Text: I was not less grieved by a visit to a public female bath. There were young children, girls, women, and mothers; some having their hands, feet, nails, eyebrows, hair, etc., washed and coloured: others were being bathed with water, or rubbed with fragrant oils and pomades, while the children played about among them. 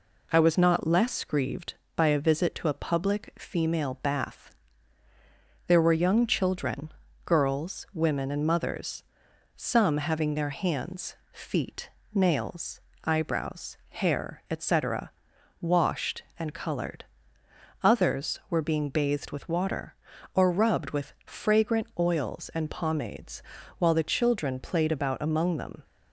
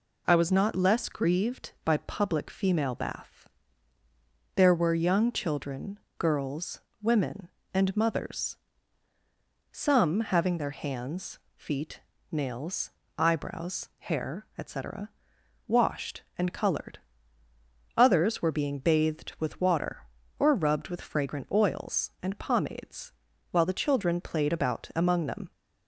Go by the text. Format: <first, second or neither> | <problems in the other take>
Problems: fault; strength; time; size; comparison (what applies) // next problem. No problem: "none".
first | skips "a visit to a"; at 1.9 s